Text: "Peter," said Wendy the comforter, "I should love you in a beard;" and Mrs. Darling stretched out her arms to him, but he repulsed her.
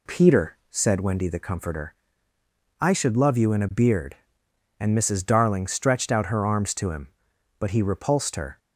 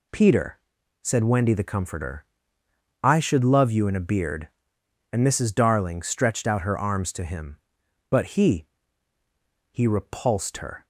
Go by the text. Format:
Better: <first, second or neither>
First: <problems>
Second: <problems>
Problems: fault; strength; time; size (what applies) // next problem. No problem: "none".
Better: first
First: none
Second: says "he" twice; at 9.6 s